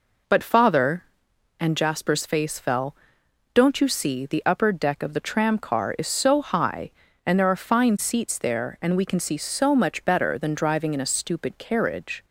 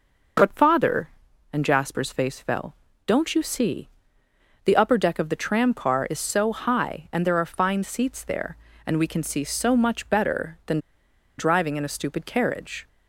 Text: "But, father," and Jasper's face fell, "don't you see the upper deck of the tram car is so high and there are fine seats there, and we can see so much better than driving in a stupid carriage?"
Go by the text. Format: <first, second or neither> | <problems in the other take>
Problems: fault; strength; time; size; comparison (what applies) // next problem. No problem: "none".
first | pauses between "see" and "the"; noticeable; at 3.8 s; 0.78 s long // pauses between "than" and "driving"; noticeable; at 10.7 s; 0.59 s long